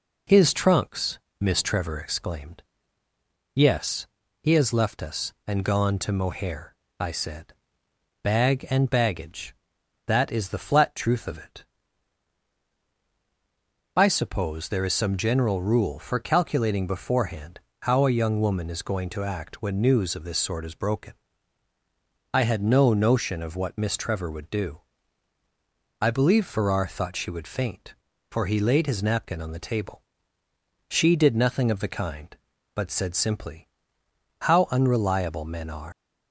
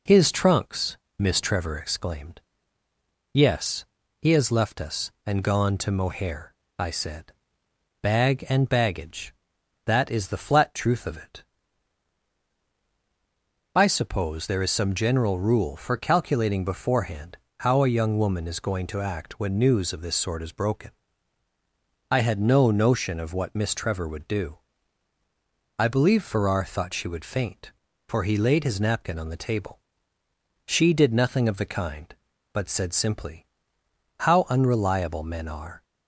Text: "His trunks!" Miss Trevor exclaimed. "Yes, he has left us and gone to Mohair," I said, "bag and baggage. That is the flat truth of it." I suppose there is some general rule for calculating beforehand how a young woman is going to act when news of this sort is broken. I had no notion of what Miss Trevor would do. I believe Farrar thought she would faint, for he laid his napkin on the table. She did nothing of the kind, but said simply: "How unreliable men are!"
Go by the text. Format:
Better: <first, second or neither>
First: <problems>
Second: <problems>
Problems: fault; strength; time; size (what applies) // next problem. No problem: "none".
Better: second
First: pauses between "beforehand" and "how"; slight; at 17.6 s; 0.22 s long // leaves "are" unfinished; at 35.9 s; 125 ms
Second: pauses between "beforehand" and "how"; slight; at 17.3 s; 0.22 s long